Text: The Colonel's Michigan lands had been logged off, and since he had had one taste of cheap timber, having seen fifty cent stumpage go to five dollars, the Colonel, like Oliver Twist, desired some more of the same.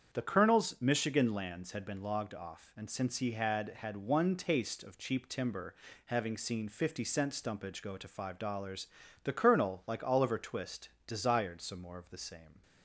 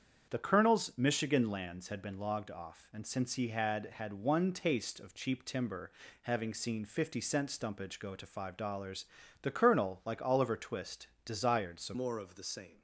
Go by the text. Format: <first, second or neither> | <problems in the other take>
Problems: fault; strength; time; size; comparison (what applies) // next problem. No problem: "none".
first | starts louder than the rest; strong; until 1.3 s; 8 dB; strong in the first // changes voice at "more"; from 11.9 s on; 0.9 s long